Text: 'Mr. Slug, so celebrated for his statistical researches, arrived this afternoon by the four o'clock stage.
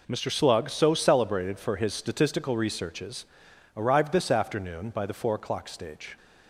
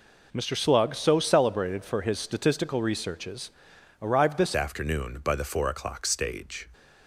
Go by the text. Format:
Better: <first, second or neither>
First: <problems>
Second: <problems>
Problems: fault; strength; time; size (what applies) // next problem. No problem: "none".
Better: first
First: none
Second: changes voice at "afternoon"; from 4.5 s on; 2.1 s long